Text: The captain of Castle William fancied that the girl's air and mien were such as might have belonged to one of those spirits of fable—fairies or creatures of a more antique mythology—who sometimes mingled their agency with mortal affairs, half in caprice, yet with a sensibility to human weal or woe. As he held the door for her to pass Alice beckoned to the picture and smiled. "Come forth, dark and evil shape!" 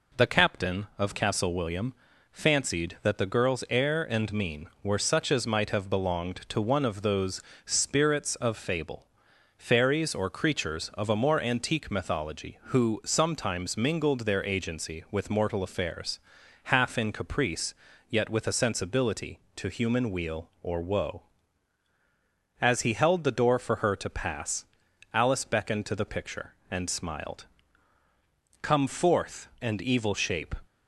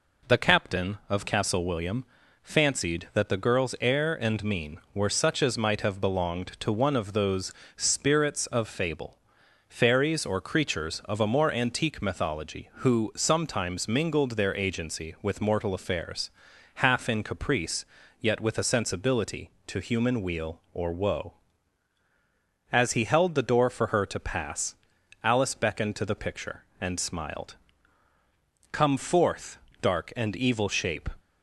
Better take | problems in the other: second | pauses between "William" and "fancied"; slight; at 1.9 s; 0.36 s long; slight in the second // pauses between "those" and "spirits"; slight; at 7.4 s; 0.24 s long; slight in the second // pauses between "pass" and "Alice"; noticeable; at 24.6 s; 0.46 s long; noticeable in the second // skips "dark"; at 29.5 s

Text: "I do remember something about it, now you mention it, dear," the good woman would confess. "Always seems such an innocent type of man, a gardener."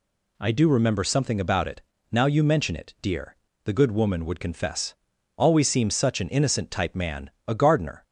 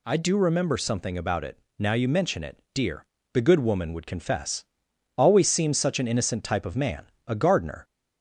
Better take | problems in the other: second | skips "of"; at 6.9 s

